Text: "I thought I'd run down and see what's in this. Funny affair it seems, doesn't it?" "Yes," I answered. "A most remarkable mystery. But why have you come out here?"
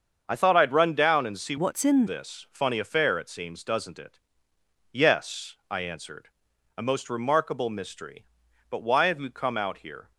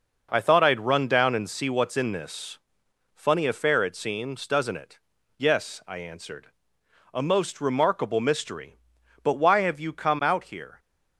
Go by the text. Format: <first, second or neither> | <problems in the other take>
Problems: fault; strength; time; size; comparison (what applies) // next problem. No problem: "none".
second | starts louder than the rest; until 1.2 s; 7 dB // changes voice from "what's" to "in"; from 1.5 to 2.0 s; 0.5 s long